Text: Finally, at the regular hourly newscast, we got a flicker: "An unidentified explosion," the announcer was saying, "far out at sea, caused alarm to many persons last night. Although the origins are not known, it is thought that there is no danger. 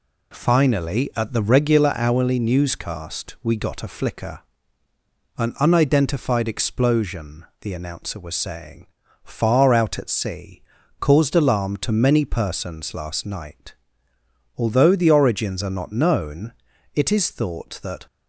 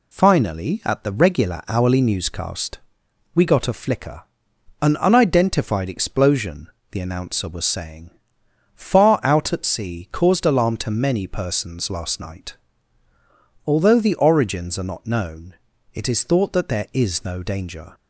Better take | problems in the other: second | stops before "there is no danger"; at 18.0 s

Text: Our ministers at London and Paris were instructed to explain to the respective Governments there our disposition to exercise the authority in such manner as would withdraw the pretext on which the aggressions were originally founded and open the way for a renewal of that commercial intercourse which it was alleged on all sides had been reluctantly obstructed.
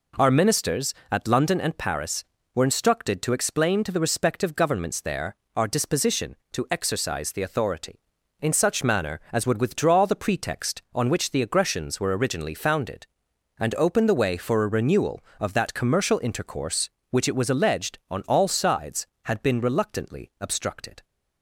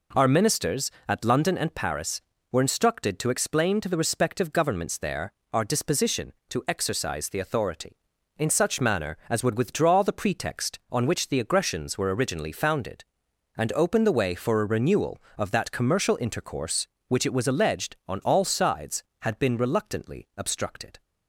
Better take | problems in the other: neither | pauses between "there" and "our"; slight; the same in both

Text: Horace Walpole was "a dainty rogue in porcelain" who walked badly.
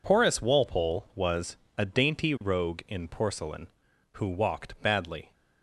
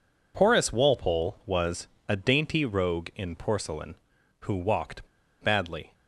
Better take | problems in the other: first | pauses between "was" and "a"; slight; at 1.8 s; 0.22 s long; slight in the first // pauses between "walked" and "badly"; slight; at 5.0 s; 0.34 s long

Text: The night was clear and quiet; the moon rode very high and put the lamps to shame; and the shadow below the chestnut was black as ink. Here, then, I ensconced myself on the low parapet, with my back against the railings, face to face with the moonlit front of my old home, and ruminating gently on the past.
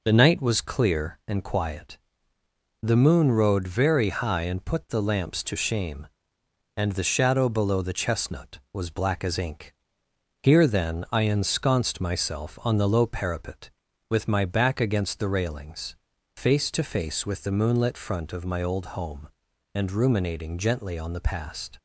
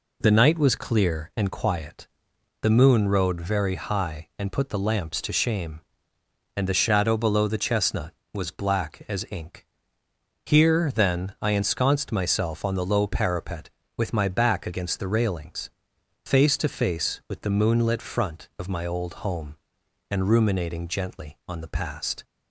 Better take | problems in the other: neither | none

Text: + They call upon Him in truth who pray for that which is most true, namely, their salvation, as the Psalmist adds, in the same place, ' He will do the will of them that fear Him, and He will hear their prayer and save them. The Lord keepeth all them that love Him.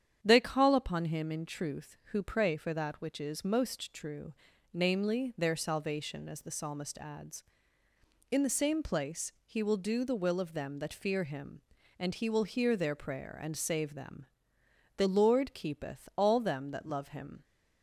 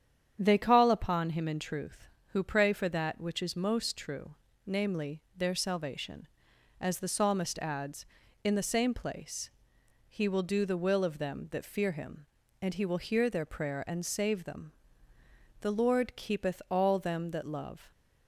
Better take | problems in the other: first | starts louder than the rest; strong; until 1.4 s; 9 dB; strong in the first // stops before "Him"; at 17.9 s

